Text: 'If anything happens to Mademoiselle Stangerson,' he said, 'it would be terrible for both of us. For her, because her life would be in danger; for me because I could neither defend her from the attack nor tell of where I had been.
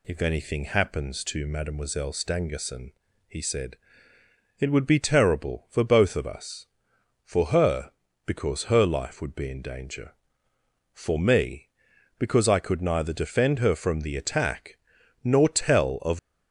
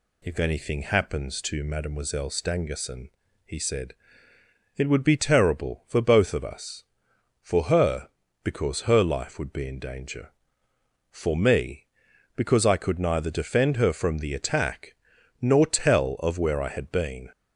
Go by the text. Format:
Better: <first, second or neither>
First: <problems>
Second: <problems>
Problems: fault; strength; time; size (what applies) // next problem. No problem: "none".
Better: second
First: pauses between "attack" and "nor"; noticeable; at 14.7 s; 0.46 s long // stops before "where I had been"; at 16.1 s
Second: pauses between "attack" and "nor"; noticeable; at 14.9 s; 0.46 s long